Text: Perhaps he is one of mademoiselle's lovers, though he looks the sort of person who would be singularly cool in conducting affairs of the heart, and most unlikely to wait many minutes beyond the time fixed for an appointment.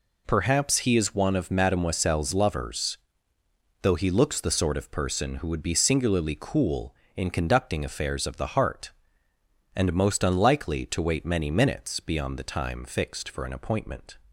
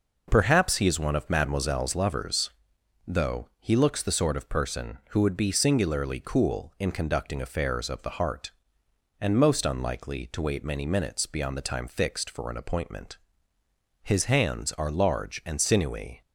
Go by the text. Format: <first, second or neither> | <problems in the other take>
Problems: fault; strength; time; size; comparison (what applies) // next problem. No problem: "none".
first | goes on to say "His hands are large and sinewy"; strong; from 14.0 s on; 2.1 s long